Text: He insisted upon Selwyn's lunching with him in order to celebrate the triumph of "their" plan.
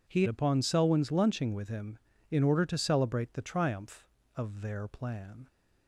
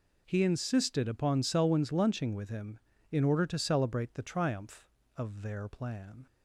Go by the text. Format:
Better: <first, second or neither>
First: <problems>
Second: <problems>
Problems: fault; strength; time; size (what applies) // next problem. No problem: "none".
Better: second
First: skips "insisted"; at 0.2 s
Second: none